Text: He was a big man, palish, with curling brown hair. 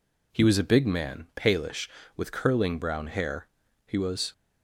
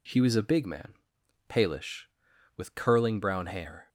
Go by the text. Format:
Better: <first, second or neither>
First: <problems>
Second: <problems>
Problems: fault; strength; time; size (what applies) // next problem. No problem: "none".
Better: second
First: goes on to say "He was"; slight; from 3.8 s on; 0.46 s long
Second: none